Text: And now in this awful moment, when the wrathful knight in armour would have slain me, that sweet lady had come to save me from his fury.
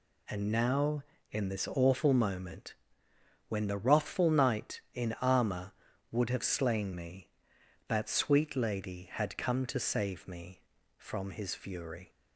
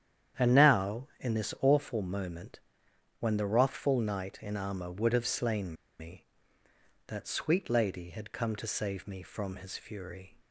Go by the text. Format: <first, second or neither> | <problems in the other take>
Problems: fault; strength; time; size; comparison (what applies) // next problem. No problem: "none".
first | starts louder than the rest; strong; until 1.5 s; 9.5 dB // pauses between "slain" and "me"; slight; at 5.7 s; 0.26 s long